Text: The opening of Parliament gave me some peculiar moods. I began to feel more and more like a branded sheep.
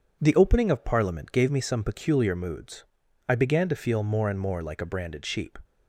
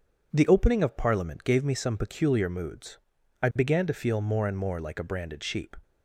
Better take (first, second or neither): neither